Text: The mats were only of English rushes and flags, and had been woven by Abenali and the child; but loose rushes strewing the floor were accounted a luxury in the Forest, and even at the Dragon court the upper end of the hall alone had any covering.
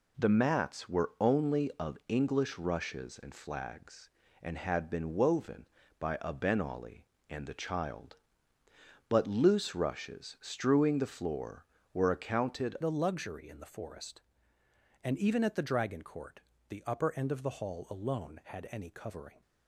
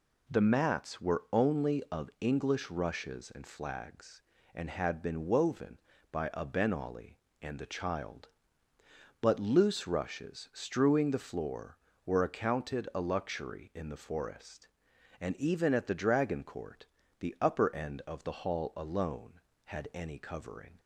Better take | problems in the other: second | changes voice at "a"; from 12.8 s on; 6.6 s long // pauses between "court" and "the"; slight; at 16.4 s; 0.26 s long; slight in the second

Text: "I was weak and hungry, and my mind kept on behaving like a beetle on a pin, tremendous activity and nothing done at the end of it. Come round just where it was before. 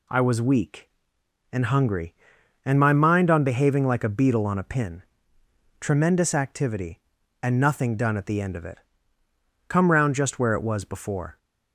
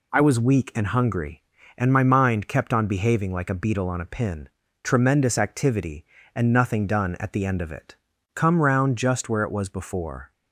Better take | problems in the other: second | skips "kept"; at 3.2 s

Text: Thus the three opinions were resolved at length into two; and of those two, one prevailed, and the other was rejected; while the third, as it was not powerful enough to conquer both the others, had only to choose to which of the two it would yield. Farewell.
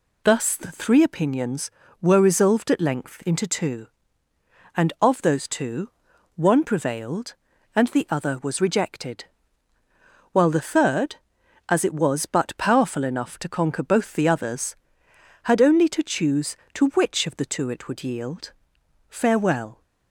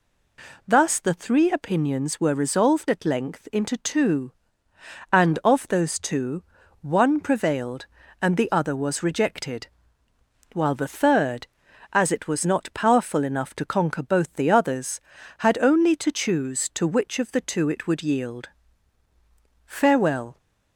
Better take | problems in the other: second | says "but" for "not"; at 12.2 s

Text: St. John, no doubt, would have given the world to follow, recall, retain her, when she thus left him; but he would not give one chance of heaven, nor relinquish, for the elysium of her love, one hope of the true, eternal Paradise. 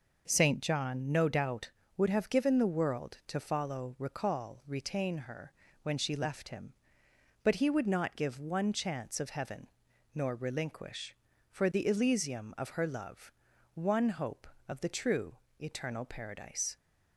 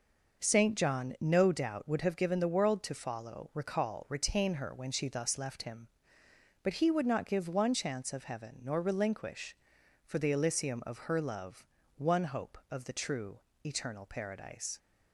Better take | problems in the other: second | skips "thus"; at 6.1 s

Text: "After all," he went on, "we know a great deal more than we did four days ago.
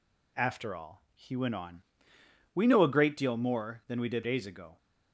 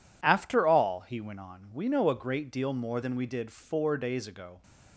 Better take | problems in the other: second | skips "four"; at 4.2 s

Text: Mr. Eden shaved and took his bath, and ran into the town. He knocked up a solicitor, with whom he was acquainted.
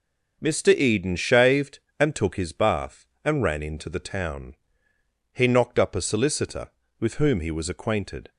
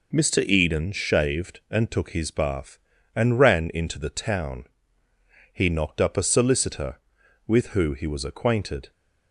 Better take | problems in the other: first | says "who" for "whom"; at 7.6 s

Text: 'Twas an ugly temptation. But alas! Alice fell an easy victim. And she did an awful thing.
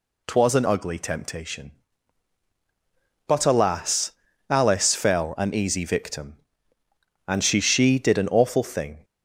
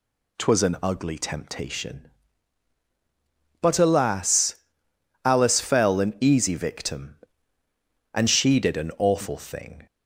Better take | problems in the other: second | says "she" twice; at 7.6 s

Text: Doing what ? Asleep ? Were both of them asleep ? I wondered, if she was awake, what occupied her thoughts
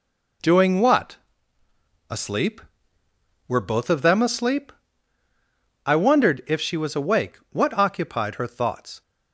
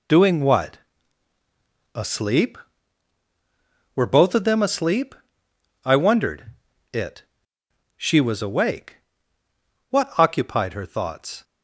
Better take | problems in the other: first | says "it" for "if"; at 6.9 s

